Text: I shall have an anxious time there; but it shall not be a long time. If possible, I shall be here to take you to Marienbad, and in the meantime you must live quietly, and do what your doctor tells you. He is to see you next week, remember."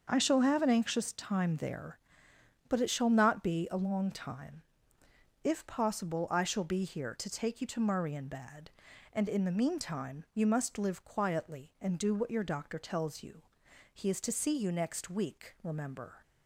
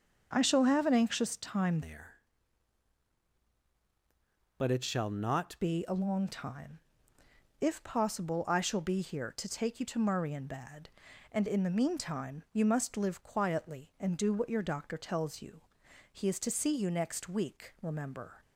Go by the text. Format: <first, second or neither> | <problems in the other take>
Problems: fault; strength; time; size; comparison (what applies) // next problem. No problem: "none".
first | starts louder than the rest; until 1.3 s; 6.5 dB; also in the first // changes voice from "there" to "not"; from 1.8 to 5.5 s; 3.7 s long